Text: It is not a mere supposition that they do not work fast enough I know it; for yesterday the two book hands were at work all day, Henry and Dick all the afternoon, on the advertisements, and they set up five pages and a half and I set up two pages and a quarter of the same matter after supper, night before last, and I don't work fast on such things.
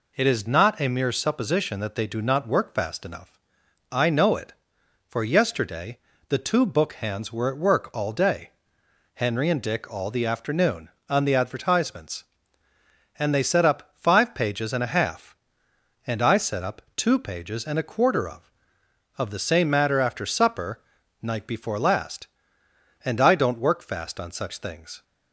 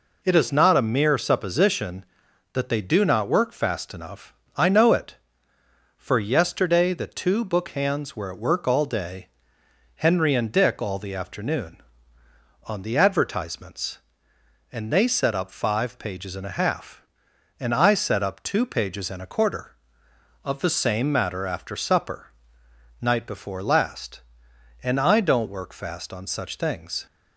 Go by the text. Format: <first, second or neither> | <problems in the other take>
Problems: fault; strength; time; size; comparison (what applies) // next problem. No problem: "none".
second | pauses between "enough" and "I"; noticeable; at 3.3 s; 0.56 s long; slight in the second // pauses between "yesterday" and "the"; slight; at 5.9 s; 0.28 s long // pauses between "up" and "two"; slight; at 16.8 s; 0.16 s long // says "of" twice; at 19.1 s